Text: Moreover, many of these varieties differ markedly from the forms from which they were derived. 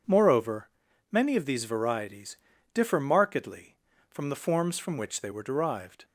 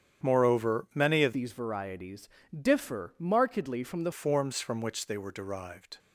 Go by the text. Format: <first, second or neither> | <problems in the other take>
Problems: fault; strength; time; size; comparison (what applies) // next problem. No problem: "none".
first | starts louder than the rest; strong; until 1.3 s; 8.5 dB // changes voice from "these" to "the"; from 1.3 to 4.1 s; 2.8 s long // pauses between "varieties" and "differ"; slight; at 2.2 s; 0.30 s long; also in the first